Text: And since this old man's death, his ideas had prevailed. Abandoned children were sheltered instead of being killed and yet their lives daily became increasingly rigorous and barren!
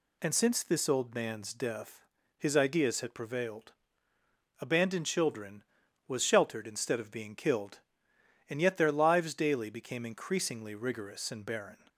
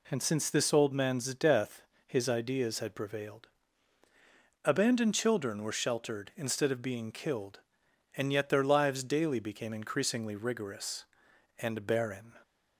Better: second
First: says "was" for "were"; at 6.0 s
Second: none

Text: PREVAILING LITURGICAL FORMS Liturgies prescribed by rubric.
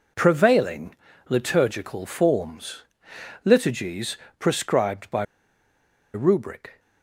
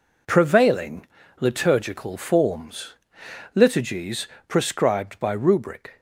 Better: second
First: pauses between "PREVAILING" and "LITURGICAL"; slight; at 0.9 s; 0.34 s long // pauses between "FORMS" and "Liturgies"; noticeable; at 2.8 s; 0.60 s long // pauses between "Liturgies" and "prescribed"; slight; at 4.1 s; 0.22 s long // pauses between "by" and "rubric"; noticeable; at 5.2 s; 0.89 s long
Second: pauses between "PREVAILING" and "LITURGICAL"; slight; at 1.0 s; 0.34 s long // pauses between "FORMS" and "Liturgies"; noticeable; at 2.9 s; 0.59 s long // pauses between "Liturgies" and "prescribed"; slight; at 4.2 s; 0.20 s long

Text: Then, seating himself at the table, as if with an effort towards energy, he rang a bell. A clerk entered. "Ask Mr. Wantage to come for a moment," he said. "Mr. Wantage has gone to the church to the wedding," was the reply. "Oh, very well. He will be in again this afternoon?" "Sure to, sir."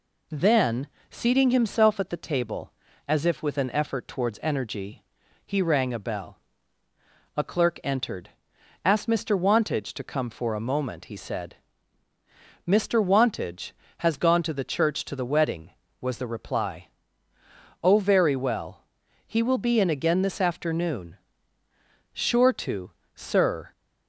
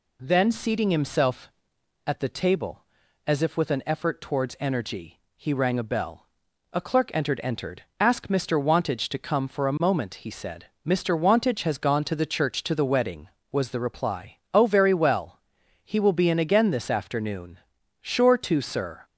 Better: first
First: none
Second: says "entered" twice; at 7.4 s

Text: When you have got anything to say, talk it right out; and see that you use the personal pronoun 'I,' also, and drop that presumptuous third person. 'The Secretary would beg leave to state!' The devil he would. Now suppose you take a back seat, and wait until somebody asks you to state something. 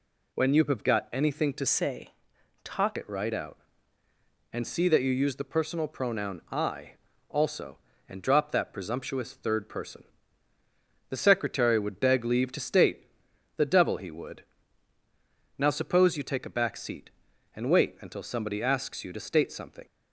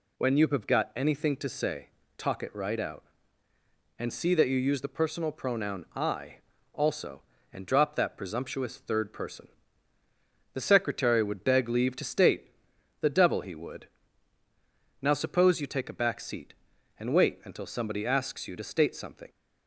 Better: second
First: changes voice from "say" to "talk"; from 1.6 to 2.9 s; 1.3 s long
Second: none

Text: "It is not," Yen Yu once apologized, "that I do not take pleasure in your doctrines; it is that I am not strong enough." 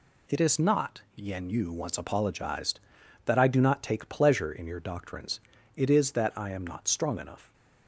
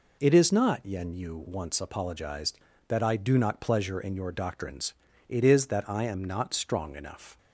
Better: first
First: none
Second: skips "take"; at 3.5 s

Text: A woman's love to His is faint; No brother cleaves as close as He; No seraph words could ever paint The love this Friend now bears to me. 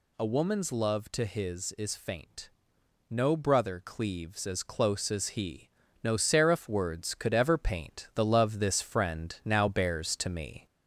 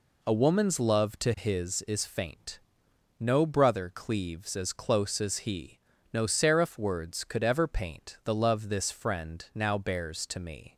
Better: second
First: gets louder; slight; throughout; 2.5 dB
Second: none

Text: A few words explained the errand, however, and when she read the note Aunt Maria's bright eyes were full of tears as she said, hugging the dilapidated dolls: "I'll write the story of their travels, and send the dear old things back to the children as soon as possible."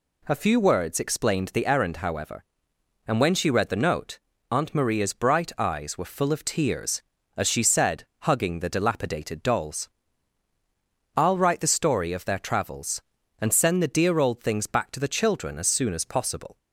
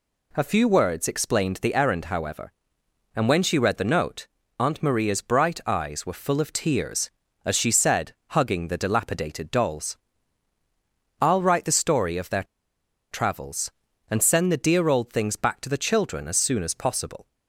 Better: first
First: pauses between "note" and "Aunt"; slight; at 4.1 s; 0.30 s long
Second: pauses between "note" and "Aunt"; slight; at 4.2 s; 0.30 s long // pauses between "their" and "travels"; noticeable; at 12.4 s; 0.67 s long

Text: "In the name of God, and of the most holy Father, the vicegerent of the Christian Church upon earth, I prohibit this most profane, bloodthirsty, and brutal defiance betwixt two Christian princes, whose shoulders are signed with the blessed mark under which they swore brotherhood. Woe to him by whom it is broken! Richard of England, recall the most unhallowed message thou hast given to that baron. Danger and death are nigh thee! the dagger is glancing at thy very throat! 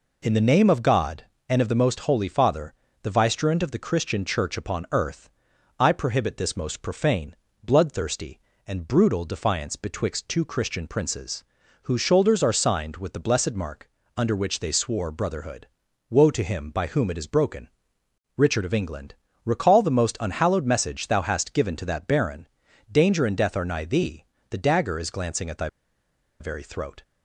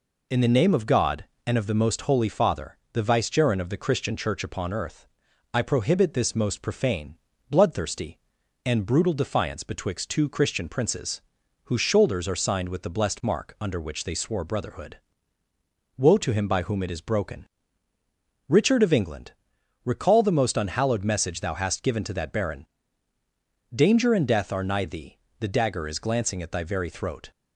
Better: second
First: pauses between "mark" and "under"; slight; at 13.8 s; 0.26 s long // pauses between "thy" and "very"; noticeable; at 25.6 s; 0.72 s long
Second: none

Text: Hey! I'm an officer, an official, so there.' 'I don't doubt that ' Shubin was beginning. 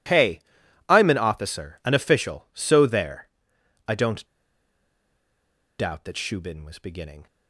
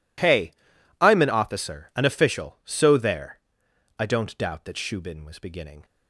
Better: second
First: pauses between "don't" and "doubt"; strong; at 4.2 s; 1.5 s long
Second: none

